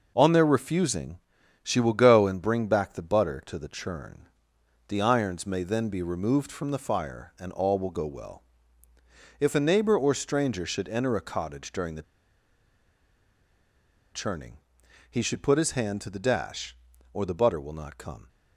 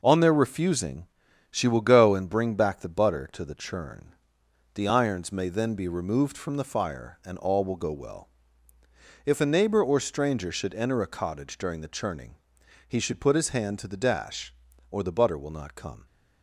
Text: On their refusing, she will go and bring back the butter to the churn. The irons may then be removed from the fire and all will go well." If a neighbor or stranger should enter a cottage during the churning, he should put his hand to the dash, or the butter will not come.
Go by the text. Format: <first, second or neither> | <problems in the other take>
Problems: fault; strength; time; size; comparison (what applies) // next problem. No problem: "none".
second | pauses between "the" and "churning"; strong; at 12.0 s; 2.1 s long